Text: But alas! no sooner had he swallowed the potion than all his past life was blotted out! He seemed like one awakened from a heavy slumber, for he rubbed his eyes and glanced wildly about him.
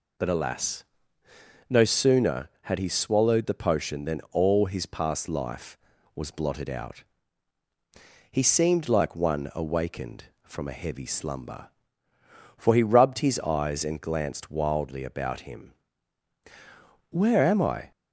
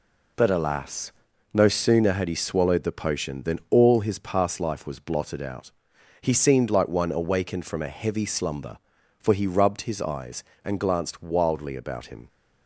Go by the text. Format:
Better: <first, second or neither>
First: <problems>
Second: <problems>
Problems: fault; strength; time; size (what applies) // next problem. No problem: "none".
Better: second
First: goes on to say "Where am I"; noticeable; from 17.1 s on; 0.80 s long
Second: none